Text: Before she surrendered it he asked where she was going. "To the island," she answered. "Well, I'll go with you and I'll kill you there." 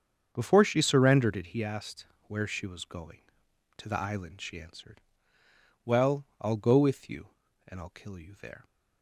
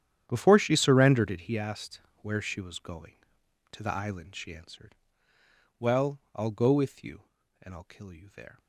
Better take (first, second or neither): first